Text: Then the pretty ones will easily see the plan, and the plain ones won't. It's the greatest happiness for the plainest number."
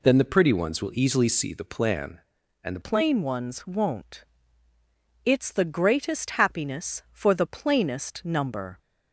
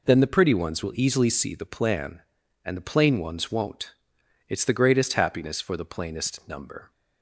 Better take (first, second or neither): second